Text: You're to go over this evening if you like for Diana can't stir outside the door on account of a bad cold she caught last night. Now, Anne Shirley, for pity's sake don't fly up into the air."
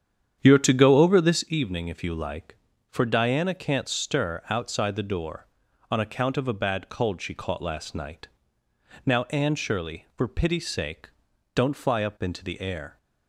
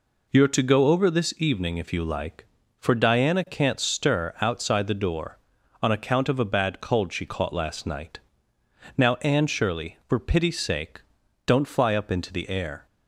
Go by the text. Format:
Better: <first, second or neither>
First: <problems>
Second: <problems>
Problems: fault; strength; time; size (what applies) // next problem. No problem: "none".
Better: second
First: starts louder than the rest; strong; until 1.6 s; 9 dB // pauses between "sake" and "don't"; at 11.1 s; 0.44 s long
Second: pauses between "sake" and "don't"; at 11.0 s; 0.44 s long